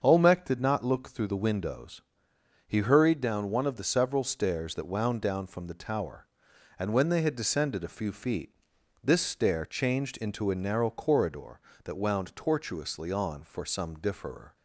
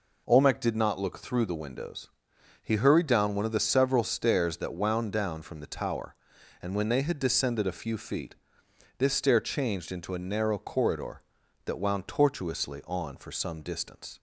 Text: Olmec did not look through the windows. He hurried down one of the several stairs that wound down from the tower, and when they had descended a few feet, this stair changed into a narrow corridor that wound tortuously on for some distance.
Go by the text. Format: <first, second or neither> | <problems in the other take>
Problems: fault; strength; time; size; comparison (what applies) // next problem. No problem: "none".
second | starts louder than the rest; until 1.0 s; 7 dB // says "differer" for "distance"; at 13.9 s